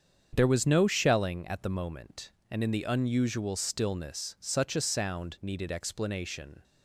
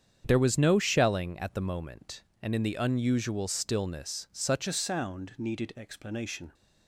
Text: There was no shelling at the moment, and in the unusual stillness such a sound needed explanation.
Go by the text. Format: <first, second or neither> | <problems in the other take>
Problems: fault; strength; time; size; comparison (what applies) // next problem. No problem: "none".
first | starts louder than the rest; strong; until 1.2 s; 8 dB; strong in the first // changes voice at "a"; from 4.6 s on; 1.9 s long